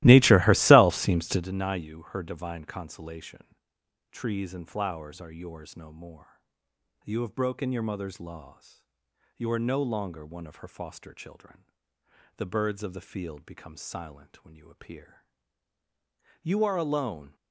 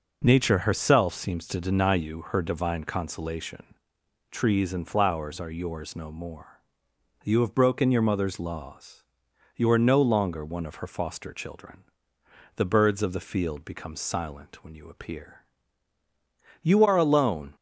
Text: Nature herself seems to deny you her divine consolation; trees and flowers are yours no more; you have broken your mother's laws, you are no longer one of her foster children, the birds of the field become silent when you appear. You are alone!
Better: second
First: starts louder than the rest; strong; until 1.5 s; 17 dB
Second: none

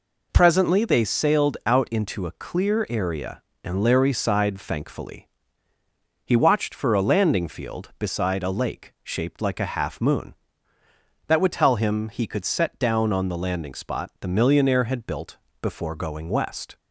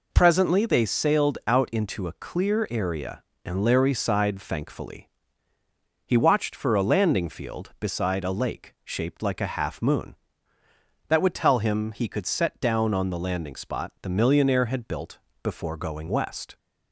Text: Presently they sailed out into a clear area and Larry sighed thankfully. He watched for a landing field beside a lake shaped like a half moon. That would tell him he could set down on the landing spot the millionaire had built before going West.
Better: neither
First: pauses between "built" and "before"; slight; at 15.3 s; 0.24 s long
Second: pauses between "built" and "before"; slight; at 15.1 s; 0.24 s long

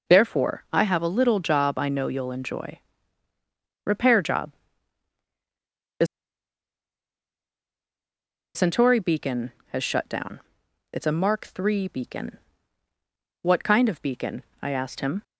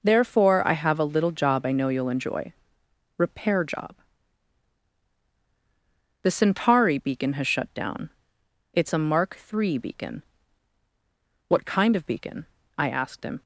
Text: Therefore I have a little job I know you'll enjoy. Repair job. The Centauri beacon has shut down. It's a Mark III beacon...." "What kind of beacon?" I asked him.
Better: second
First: pauses between "The" and "Centauri"; strong; at 6.0 s; 2.4 s long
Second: none

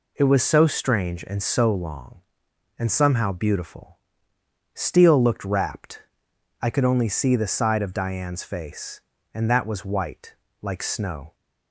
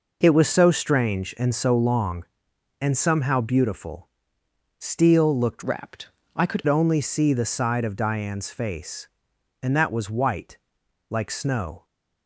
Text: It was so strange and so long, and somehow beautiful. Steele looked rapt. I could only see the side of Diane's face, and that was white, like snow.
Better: first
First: none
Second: changes voice from "rapt" to "could"; from 5.6 to 6.6 s; 1.0 s long

